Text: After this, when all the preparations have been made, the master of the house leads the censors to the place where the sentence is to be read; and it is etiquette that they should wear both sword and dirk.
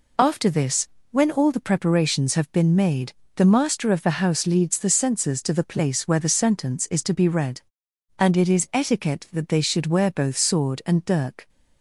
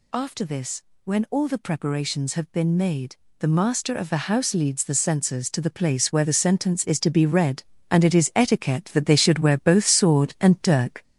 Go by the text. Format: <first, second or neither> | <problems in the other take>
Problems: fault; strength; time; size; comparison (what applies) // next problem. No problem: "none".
first | gets louder; noticeable; throughout; 5.5 dB